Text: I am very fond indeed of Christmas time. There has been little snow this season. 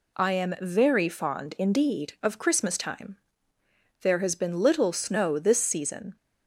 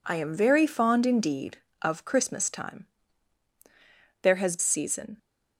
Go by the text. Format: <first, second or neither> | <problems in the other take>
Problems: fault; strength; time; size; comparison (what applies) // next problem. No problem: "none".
first | skips "been little snow this"; at 4.5 s